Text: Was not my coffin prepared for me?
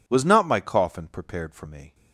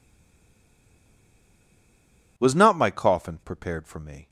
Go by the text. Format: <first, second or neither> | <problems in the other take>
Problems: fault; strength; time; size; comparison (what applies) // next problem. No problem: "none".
first | stays silent before the first word; until 2.3 s; 2.3 s long